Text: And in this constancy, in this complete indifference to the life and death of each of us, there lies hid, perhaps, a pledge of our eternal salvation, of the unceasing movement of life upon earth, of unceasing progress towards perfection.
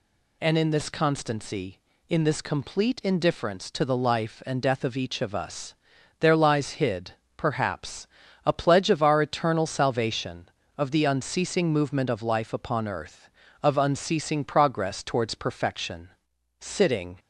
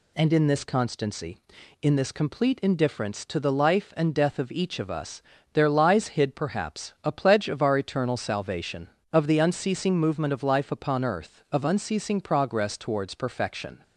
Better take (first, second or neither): second